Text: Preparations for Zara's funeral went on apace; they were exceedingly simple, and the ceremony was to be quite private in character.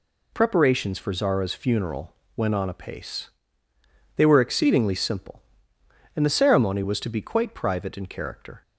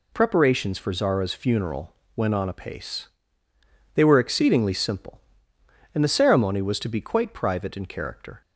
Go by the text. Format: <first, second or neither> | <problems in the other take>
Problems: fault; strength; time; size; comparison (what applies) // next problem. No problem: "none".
neither | pauses between "funeral" and "went"; slight; the same in both